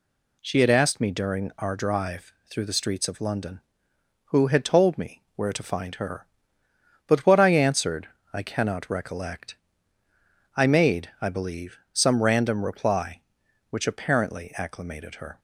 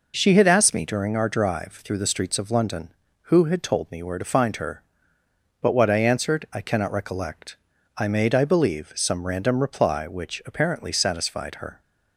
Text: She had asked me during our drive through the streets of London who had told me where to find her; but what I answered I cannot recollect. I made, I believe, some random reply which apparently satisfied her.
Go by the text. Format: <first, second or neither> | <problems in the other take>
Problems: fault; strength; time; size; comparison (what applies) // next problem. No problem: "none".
second | pauses between "drive" and "through"; slight; at 2.3 s; 0.16 s long // pauses between "answered" and "I"; slight; at 8.0 s; 0.26 s long // says "acclimated" for "satisfied"; at 14.5 s